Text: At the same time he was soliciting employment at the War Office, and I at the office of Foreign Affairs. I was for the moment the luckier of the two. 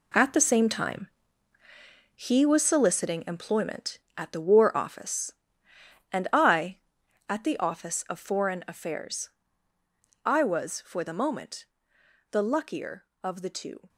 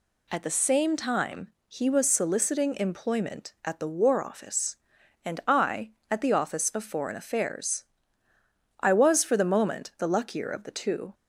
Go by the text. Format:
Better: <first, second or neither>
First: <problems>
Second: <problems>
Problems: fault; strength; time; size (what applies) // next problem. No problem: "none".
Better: second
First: gets quieter; strong; throughout; 10.5 dB // pauses between "time" and "he"; at 1.0 s; 1.0 s long // pauses between "moment" and "the"; noticeable; at 11.6 s; 0.66 s long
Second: pauses between "time" and "he"; slight; at 1.5 s; 0.16 s long